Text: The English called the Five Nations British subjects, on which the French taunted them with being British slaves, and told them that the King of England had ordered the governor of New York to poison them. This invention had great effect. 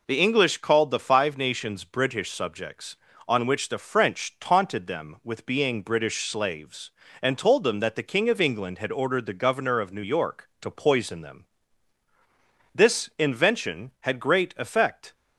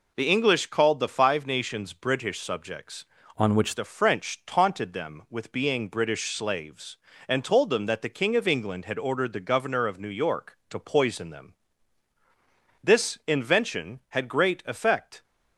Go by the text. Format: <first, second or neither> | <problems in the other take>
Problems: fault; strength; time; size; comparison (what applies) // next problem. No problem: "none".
first | changes voice from "on" to "which"; from 3.3 to 3.7 s; 0.4 s long